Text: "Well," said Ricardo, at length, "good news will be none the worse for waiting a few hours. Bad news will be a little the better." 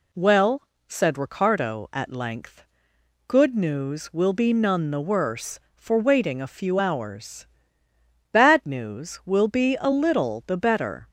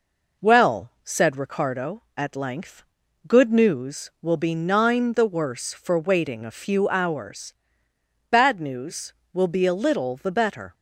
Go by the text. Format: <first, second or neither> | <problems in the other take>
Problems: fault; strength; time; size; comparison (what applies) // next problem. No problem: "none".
first | says "nine" for "none"; at 4.5 s